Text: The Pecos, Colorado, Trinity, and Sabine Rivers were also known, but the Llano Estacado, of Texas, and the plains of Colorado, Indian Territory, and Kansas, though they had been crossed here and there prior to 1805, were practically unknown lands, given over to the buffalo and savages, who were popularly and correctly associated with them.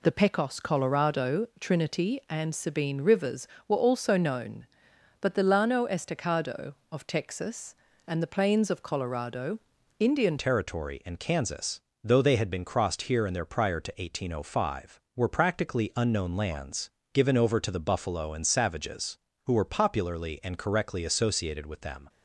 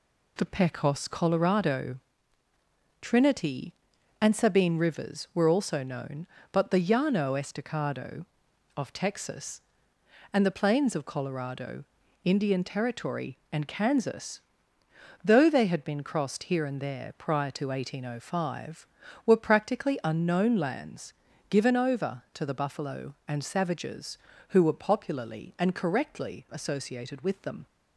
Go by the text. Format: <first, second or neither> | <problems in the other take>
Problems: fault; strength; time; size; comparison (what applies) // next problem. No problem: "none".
second | changes voice at "Territory"; from 10.3 s on; 11.7 s long